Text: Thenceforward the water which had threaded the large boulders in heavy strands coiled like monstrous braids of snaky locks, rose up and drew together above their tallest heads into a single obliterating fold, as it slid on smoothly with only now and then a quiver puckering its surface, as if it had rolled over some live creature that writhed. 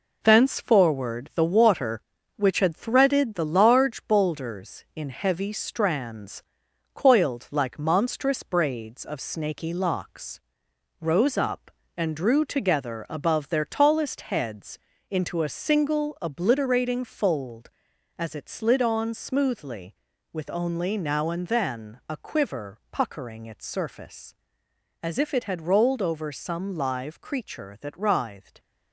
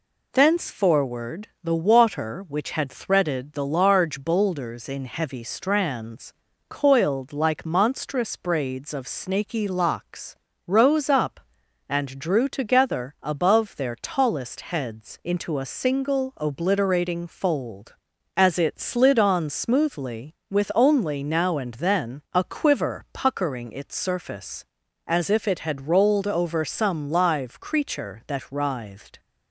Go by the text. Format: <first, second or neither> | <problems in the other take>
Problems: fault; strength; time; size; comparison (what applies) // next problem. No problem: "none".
second | gets quieter; noticeable; throughout; 6 dB // pauses between "strands" and "coiled"; noticeable; at 6.4 s; 0.50 s long; also in the second // pauses between "heads" and "into"; slight; at 14.7 s; 0.32 s long